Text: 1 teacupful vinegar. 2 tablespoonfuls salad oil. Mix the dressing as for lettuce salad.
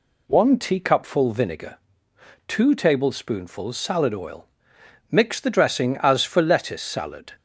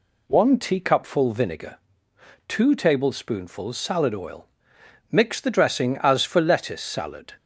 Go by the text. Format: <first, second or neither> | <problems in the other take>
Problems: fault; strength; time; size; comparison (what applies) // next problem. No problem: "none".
neither | none